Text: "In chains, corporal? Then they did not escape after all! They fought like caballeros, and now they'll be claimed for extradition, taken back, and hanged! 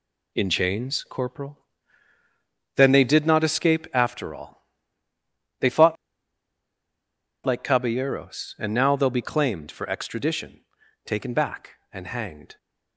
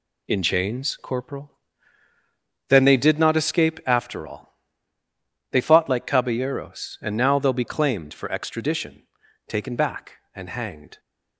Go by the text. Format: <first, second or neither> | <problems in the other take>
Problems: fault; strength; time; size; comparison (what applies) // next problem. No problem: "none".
second | pauses between "fought" and "like"; strong; at 5.9 s; 1.4 s long